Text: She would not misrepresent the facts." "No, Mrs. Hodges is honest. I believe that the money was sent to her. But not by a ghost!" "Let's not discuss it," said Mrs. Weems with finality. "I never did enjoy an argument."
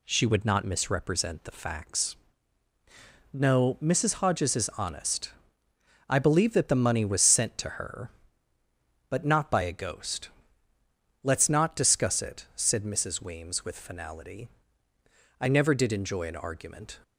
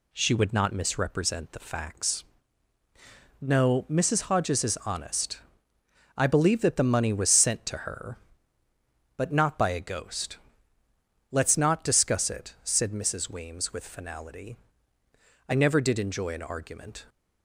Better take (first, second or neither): neither